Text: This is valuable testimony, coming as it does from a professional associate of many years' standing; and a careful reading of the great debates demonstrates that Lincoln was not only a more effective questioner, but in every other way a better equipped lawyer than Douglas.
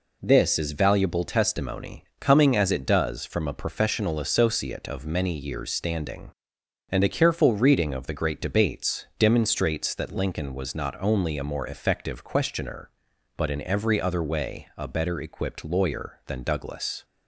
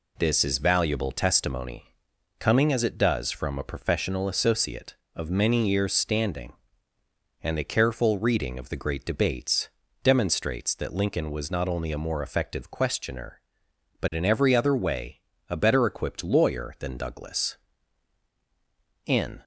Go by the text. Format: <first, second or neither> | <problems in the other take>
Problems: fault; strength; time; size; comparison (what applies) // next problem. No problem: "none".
first | pauses between "debates" and "demonstrates"; slight; at 9.6 s; 0.36 s long // pauses between "way" and "a"; slight; at 15.2 s; 0.28 s long // goes on to say "In"; slight; from 19.0 s on; 0.38 s long